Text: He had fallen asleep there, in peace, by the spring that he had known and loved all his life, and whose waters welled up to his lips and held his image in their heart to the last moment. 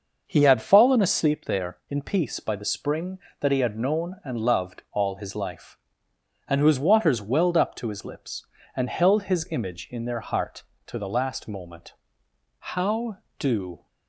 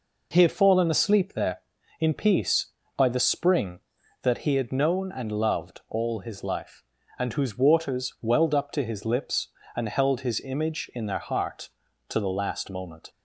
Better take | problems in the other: second | starts louder than the rest; noticeable; until 1.2 s; 6 dB // goes on to say "How do"; noticeable; from 12.5 s on; 1.2 s long

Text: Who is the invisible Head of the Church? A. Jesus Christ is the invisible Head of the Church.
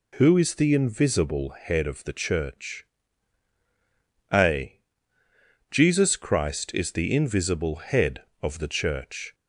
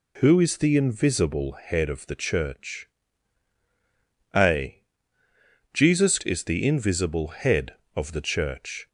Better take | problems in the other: first | skips "Christ"; at 6.2 s

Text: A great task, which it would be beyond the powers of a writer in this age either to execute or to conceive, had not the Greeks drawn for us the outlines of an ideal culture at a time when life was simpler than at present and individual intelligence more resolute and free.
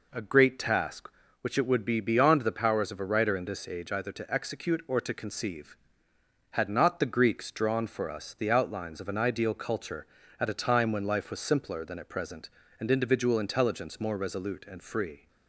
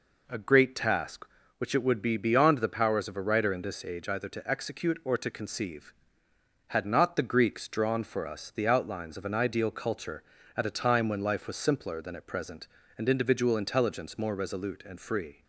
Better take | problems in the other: neither | none

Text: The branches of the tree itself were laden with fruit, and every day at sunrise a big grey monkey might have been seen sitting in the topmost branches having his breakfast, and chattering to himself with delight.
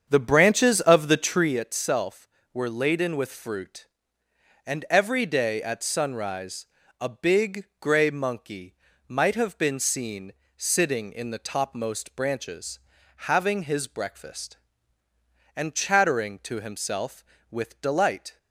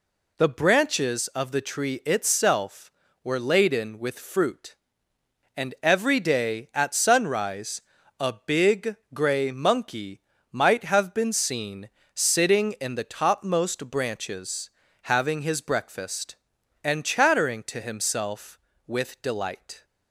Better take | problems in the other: second | starts louder than the rest; strong; until 1.6 s; 7.5 dB // pauses between "sunrise" and "a"; slight; at 6.6 s; 0.36 s long; also in the second // pauses between "big" and "grey"; slight; at 7.6 s; 0.16 s long; slight in the second // pauses between "monkey" and "might"; slight; at 8.7 s; 0.36 s long; slight in the second // pauses between "seen" and "sitting"; slight; at 10.3 s; 0.24 s long; slight in the second // pauses between "branches" and "having"; at 12.7 s; 0.42 s long; slight in the second

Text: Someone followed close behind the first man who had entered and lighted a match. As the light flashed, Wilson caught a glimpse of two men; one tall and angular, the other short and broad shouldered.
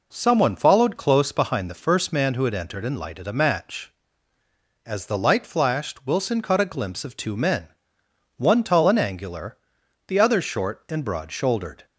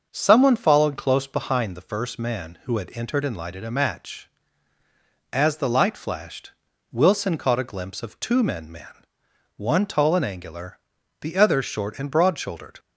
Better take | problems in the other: first | starts louder than the rest; until 1.1 s; 6 dB // says "men" twice; at 8.7 s

